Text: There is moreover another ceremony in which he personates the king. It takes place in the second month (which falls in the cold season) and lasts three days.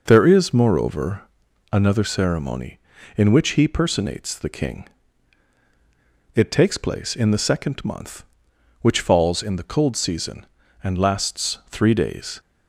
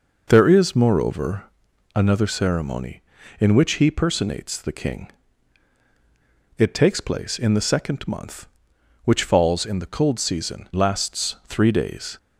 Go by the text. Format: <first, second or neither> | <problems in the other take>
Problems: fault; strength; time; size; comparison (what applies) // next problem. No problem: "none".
first | pauses between "moreover" and "another"; noticeable; at 1.4 s; 0.50 s long; noticeable in the first // skips "and"; at 10.7 s